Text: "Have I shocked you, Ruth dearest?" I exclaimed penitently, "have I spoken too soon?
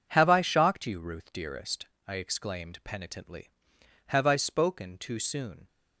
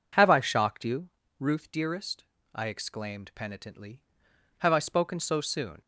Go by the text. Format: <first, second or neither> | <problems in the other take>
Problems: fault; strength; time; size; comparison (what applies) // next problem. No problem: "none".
first | says "so" for "too"; at 5.1 s